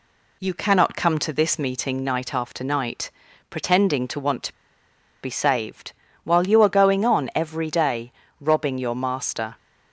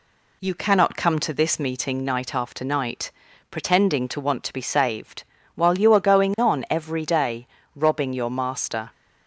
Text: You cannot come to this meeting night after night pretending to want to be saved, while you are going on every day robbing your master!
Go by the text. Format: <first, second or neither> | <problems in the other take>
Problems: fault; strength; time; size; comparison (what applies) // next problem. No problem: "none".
second | pauses between "night" and "pretending"; at 3.1 s; 0.40 s long; also in the second // pauses between "to" and "be"; noticeable; at 4.5 s; 0.70 s long // pauses between "day" and "robbing"; slight; at 8.1 s; 0.30 s long; slight in the second